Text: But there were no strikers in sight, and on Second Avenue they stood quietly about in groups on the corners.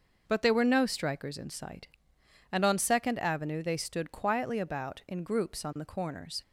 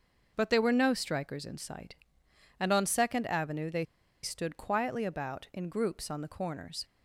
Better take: first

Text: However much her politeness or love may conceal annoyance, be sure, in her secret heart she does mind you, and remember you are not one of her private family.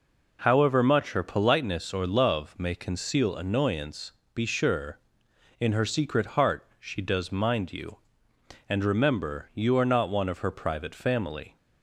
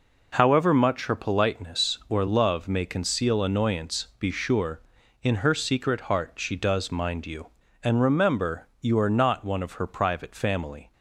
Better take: neither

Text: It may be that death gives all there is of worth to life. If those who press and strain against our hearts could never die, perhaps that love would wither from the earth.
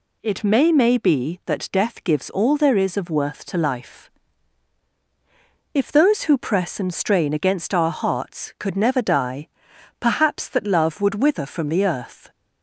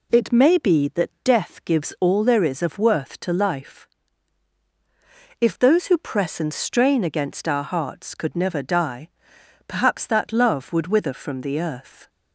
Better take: second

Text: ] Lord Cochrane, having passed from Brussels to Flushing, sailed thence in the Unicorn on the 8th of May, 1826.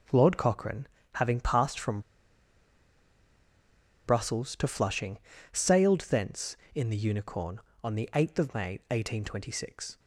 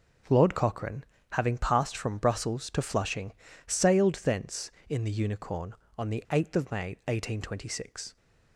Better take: second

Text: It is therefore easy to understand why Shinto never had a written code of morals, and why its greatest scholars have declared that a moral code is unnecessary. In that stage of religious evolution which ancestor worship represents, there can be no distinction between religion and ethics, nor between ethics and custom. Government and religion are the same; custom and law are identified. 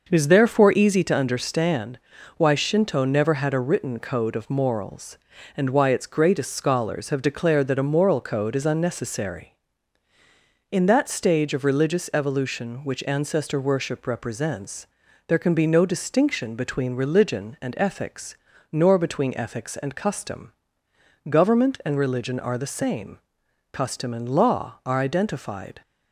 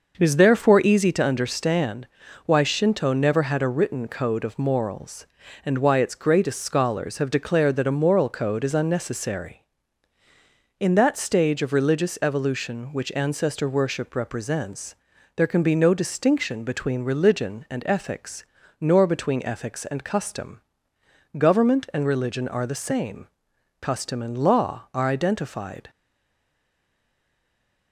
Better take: first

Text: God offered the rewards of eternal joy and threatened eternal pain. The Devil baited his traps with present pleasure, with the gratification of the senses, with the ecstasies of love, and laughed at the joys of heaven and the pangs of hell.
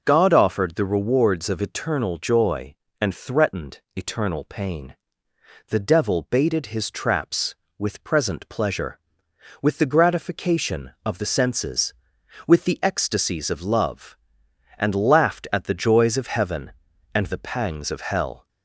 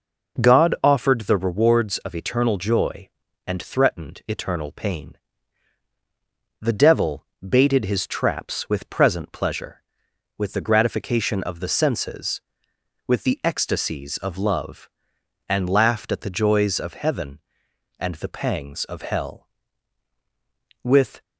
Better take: first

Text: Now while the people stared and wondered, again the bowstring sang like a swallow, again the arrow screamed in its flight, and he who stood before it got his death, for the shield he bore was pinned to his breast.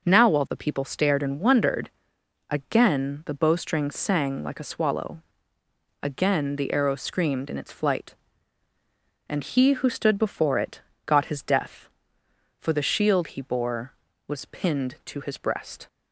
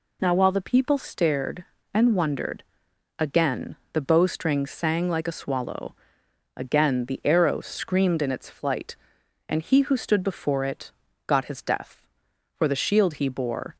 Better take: first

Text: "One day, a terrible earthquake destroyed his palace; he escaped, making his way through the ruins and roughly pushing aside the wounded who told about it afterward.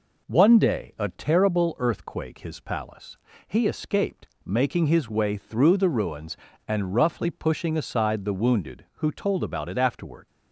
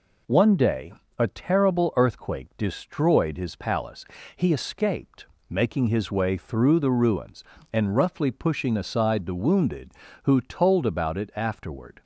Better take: second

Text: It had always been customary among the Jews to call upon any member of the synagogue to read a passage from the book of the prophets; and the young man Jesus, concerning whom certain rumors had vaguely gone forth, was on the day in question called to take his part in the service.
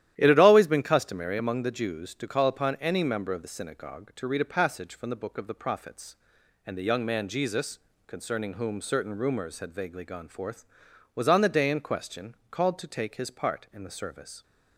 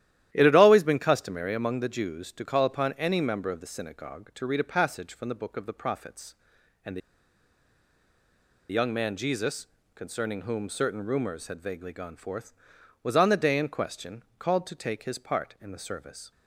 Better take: first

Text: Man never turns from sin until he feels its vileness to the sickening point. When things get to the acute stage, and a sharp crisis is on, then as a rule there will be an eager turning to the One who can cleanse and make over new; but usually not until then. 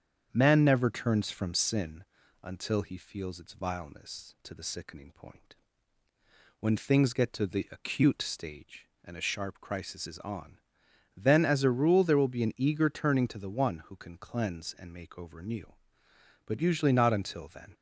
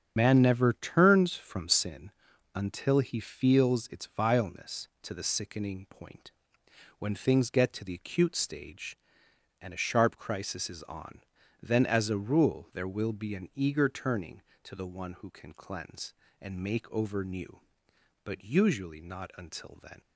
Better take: first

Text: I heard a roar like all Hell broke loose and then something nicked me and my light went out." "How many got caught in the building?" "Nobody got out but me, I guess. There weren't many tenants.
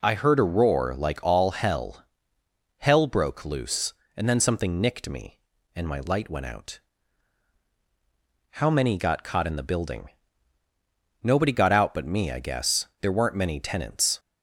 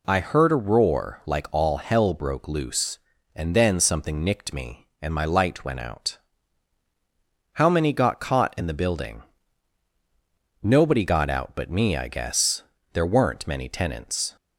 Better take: second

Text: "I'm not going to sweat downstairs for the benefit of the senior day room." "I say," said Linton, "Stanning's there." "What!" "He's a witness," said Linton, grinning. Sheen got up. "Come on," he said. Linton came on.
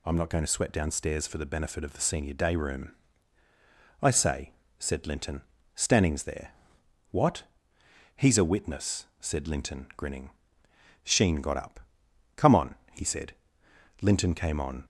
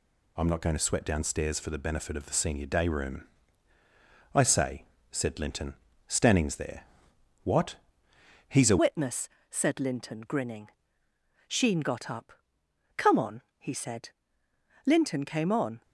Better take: first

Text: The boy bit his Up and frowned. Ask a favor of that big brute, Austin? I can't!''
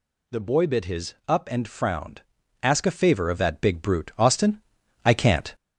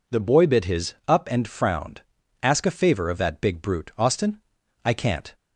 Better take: second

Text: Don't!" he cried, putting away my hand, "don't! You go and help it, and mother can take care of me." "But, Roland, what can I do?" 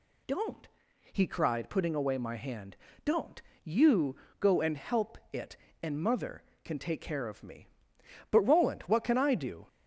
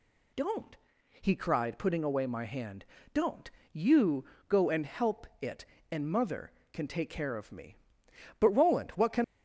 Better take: first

